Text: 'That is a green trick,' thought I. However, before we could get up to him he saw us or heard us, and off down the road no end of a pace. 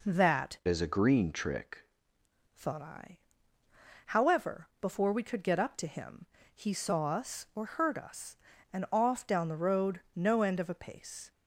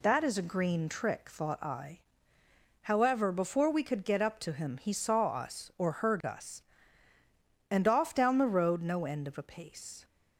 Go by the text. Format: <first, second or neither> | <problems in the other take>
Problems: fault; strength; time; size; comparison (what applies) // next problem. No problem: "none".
second | changes voice from "is" to "trick"; from 0.6 to 1.8 s; 1.2 s long // pauses between "him" and "he"; slight; at 6.2 s; 0.30 s long